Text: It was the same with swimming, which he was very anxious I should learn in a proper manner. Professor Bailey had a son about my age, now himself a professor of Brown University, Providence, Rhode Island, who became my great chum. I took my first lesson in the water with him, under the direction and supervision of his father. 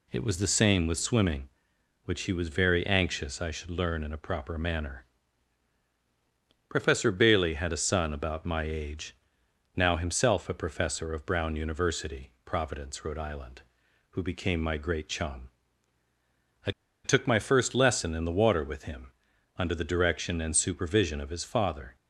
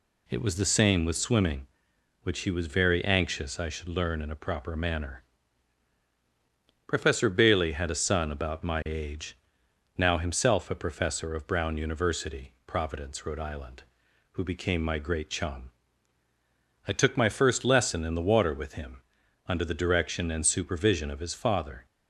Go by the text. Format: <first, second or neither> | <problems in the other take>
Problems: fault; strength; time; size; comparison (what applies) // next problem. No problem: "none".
second | pauses between "I" and "took"; slight; at 16.6 s; 0.34 s long